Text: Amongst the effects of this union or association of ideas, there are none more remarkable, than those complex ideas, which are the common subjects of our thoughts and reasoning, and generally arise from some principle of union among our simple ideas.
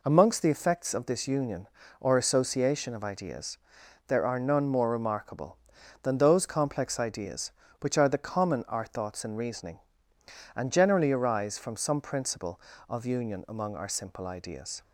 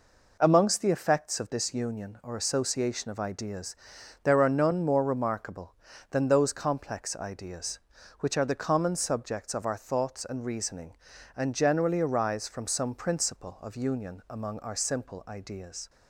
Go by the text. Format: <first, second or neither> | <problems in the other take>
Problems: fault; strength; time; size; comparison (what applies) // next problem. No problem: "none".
second | skips "subjects of"; at 8.6 s